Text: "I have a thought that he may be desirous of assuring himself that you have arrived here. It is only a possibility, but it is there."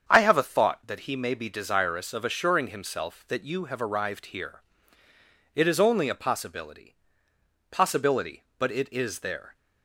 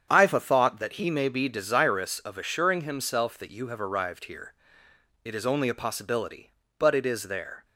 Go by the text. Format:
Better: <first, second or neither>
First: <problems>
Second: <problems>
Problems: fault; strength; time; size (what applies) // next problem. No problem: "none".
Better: second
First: starts louder than the rest; strong; until 1.0 s; 7.5 dB // says "possibility" twice; at 7.7 s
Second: starts louder than the rest; strong; until 1.0 s; 8 dB